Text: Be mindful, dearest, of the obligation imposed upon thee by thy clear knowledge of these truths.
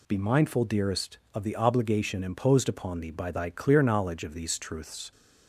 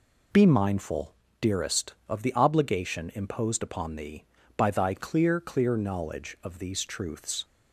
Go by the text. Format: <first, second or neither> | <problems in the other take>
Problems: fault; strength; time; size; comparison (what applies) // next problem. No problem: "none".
first | says "clear" twice; at 5.4 s